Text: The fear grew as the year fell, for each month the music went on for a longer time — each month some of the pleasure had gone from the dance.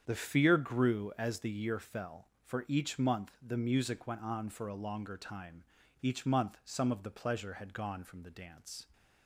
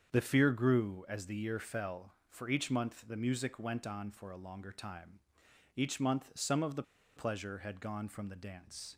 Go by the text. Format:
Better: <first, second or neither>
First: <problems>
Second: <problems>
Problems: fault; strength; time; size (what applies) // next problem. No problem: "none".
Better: first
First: starts louder than the rest; strong; until 1.0 s; 8 dB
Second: starts louder than the rest; strong; until 1.1 s; 7.5 dB // pauses between "the" and "pleasure"; slight; at 6.8 s; 0.34 s long